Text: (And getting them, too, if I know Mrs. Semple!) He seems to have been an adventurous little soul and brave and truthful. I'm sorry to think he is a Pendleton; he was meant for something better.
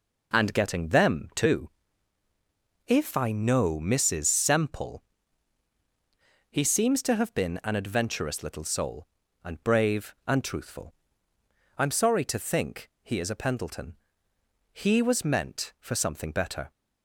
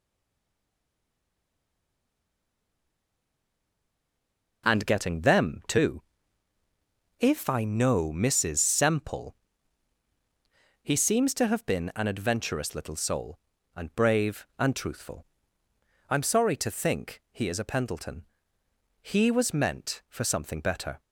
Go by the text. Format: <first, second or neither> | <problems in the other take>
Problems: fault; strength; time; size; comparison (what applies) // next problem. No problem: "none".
first | stays silent before the first word; strong; until 4.6 s; 4.6 s long